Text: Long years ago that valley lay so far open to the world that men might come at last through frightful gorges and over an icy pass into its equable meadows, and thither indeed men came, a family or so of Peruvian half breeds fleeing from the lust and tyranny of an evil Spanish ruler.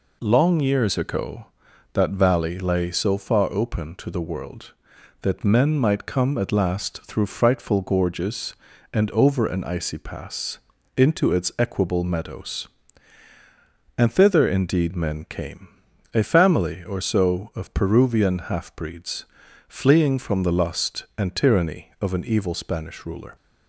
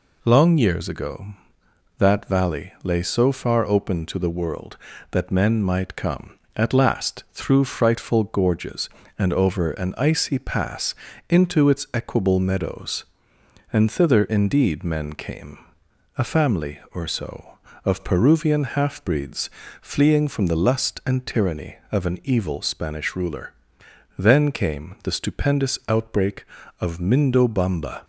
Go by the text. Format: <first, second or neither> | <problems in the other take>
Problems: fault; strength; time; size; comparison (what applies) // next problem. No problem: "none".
first | pauses between "pass" and "into"; slight; at 10.9 s; 0.34 s long; also in the first // pauses between "breeds" and "fleeing"; slight; at 19.4 s; 0.32 s long; also in the first // goes on to say "Then came the stupendous outbreak of Mindobamba"; strong; from 24.1 s on; 3.8 s long